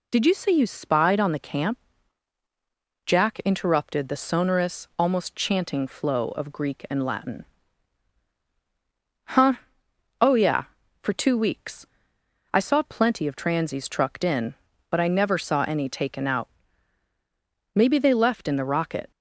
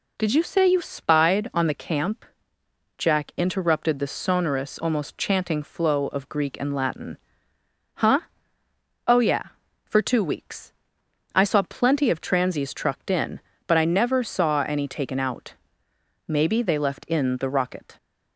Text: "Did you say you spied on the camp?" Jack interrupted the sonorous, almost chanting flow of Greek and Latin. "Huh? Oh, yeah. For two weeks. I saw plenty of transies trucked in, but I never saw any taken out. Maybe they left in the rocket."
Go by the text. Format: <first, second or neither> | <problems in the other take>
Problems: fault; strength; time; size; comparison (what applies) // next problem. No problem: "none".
neither | none